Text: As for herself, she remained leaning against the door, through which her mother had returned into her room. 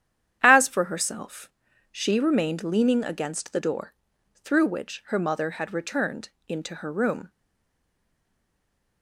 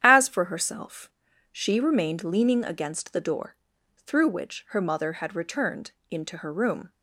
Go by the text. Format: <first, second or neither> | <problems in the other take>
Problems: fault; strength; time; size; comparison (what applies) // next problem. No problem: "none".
second | starts louder than the rest; strong; until 1.4 s; 10 dB; strong in the second // pauses between "returned" and "into"; slight; at 6.2 s; 0.18 s long; slight in the second // stays silent after the last word; noticeable; from 7.2 s on; 1.8 s long